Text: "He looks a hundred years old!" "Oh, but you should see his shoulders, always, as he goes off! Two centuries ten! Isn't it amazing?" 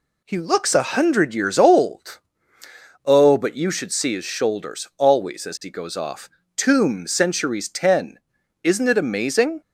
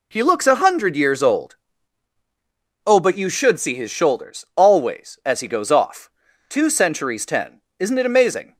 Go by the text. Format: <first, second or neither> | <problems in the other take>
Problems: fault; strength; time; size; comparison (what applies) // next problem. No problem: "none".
second | says "Tomb" for "Two"; at 6.5 s